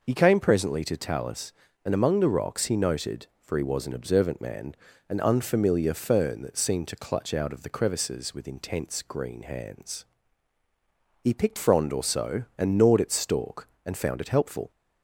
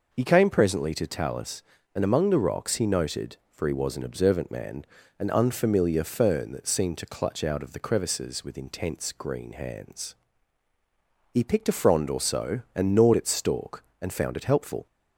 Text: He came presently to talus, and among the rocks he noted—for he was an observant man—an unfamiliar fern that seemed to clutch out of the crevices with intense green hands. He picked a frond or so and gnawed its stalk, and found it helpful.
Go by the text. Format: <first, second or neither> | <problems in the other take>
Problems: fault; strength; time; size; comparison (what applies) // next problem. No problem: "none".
second | skips "a"; at 11.5 s